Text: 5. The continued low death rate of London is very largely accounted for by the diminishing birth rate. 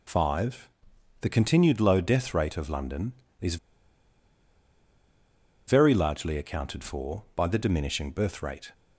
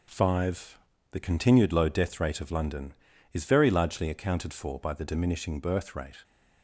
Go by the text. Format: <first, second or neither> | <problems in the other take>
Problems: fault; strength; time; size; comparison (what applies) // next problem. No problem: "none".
second | pauses between "is" and "very"; strong; at 3.5 s; 2.1 s long